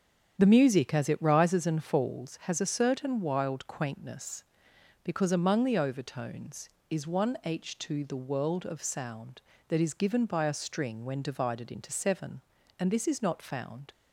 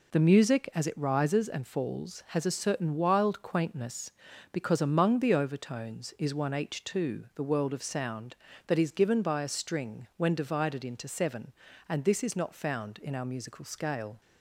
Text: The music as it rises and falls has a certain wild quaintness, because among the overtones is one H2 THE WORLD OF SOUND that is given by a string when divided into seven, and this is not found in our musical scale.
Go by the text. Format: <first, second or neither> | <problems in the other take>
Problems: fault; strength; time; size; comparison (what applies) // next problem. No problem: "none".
second | starts louder than the rest; strong; until 1.3 s; 8 dB // stops before "in our musical scale"; at 13.9 s